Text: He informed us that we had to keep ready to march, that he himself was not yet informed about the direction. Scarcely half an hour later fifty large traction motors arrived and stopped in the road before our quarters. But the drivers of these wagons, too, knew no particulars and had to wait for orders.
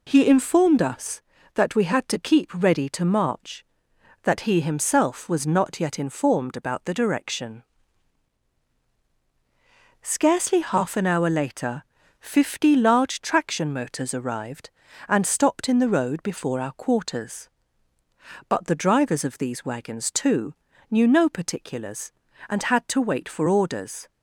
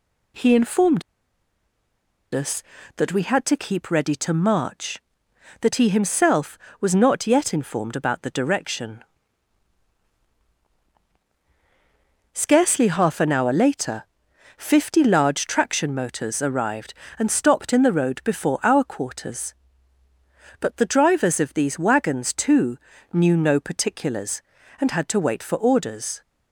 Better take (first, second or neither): first